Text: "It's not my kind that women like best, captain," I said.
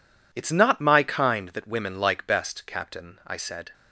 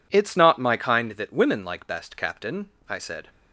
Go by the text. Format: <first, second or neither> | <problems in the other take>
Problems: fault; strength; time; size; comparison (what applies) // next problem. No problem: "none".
neither | none